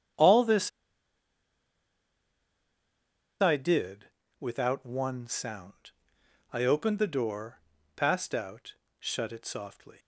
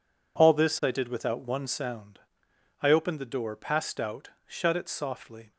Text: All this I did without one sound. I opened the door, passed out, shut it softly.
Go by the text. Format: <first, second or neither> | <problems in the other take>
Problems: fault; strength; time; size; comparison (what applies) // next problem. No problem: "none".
second | starts louder than the rest; strong; until 3.8 s; 9 dB // pauses between "this" and "I"; strong; at 0.6 s; 2.7 s long // pauses between "did" and "without"; slight; at 4.0 s; 0.34 s long